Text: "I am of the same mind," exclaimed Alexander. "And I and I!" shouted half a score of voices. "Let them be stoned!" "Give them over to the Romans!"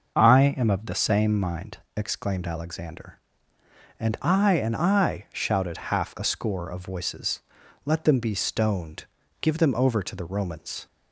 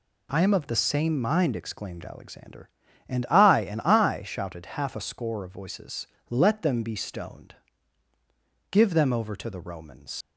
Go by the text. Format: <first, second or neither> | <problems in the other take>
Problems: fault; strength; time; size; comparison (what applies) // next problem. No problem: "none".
first | leaves "Romans" unfinished; at 10.2 s; 95 ms